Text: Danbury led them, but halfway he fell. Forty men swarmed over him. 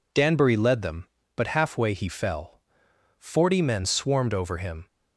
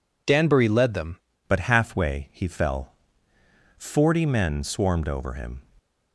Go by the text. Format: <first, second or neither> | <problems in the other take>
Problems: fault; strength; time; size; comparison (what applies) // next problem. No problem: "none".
first | changes voice at "but"; from 1.4 s on; 4.1 s long